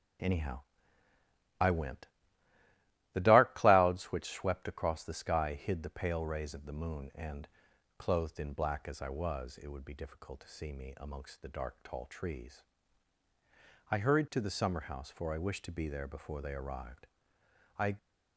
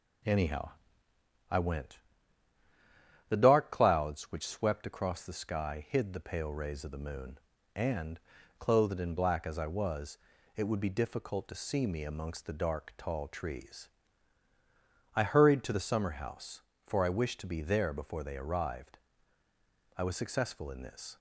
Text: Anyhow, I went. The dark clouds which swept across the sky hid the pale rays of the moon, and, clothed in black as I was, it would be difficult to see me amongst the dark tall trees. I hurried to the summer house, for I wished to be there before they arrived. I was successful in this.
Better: second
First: stops before "was successful in this"; at 17.9 s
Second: none

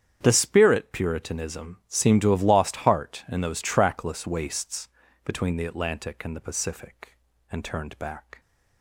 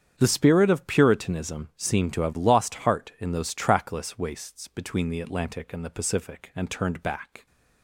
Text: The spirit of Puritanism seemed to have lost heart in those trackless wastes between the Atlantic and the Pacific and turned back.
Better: second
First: starts louder than the rest; strong; until 1.2 s; 8.5 dB // skips "of"; at 0.9 s // pauses between "wastes" and "between"; slight; at 4.8 s; 0.36 s long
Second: starts louder than the rest; strong; until 1.1 s; 8 dB

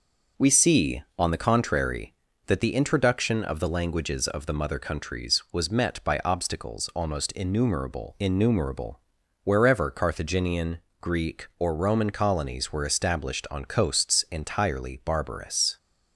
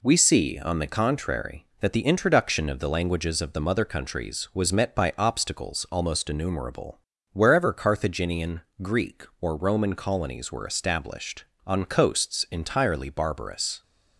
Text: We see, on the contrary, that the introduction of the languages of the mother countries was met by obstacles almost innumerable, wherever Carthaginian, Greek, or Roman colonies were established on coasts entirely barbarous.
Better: second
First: says "innumerable" twice; at 8.1 s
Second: none

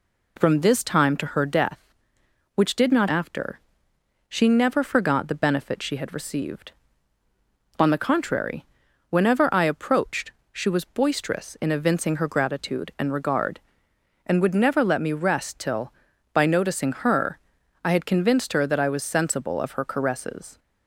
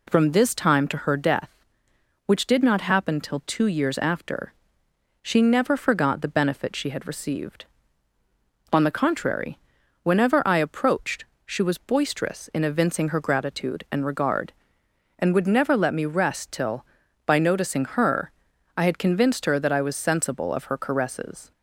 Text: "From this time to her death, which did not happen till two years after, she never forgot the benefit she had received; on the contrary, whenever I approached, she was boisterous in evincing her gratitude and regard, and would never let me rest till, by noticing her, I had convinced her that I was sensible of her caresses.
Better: second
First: skips "happen till two years"; at 3.0 s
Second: none

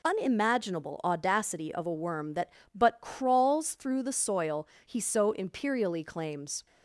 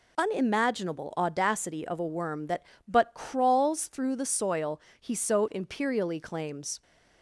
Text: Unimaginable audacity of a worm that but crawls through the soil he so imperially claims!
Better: neither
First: pauses between "soil" and "he"; slight; at 4.6 s; 0.21 s long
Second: pauses between "soil" and "he"; slight; at 4.7 s; 0.22 s long

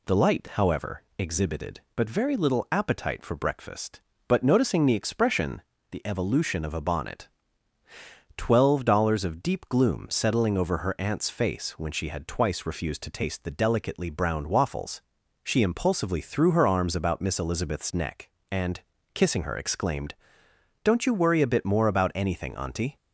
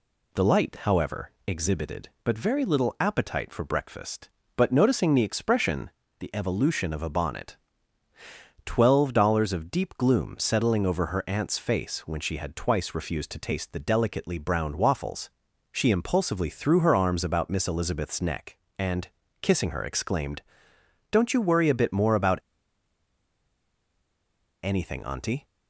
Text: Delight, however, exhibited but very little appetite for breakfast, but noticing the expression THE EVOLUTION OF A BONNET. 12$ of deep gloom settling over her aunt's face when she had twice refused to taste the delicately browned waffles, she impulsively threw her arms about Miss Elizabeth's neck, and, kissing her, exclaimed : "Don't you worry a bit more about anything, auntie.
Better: first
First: pauses between "expression" and "THE"; slight; at 5.6 s; 0.30 s long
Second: pauses between "expression" and "THE"; slight; at 5.8 s; 0.30 s long // pauses between "about" and "anything"; strong; at 22.3 s; 2.2 s long

